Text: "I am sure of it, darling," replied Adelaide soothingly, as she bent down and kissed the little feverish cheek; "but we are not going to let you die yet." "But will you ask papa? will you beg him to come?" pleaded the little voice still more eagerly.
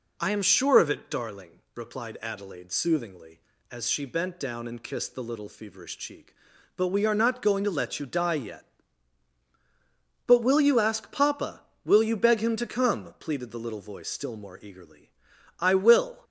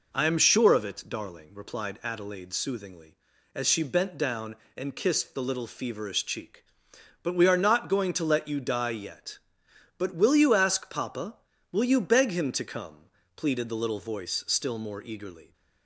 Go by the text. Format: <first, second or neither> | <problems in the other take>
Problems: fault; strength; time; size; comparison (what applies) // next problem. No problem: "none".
second | goes on to say "I will"; noticeable; from 15.5 s on; 0.64 s long